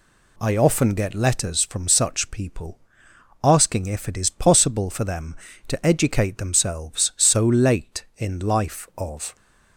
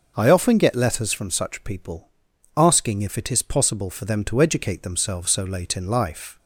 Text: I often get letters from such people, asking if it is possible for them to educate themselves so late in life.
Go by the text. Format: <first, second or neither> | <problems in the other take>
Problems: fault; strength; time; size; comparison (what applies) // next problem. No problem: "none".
second | goes on to say "Of"; slight; from 8.9 s on; 0.38 s long